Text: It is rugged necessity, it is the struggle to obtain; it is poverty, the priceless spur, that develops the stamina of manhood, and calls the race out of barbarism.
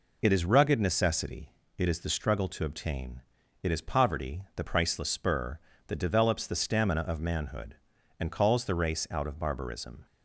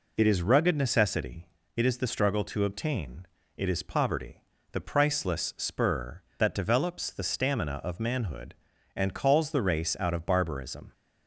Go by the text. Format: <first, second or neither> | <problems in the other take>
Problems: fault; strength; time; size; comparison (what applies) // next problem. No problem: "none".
neither | none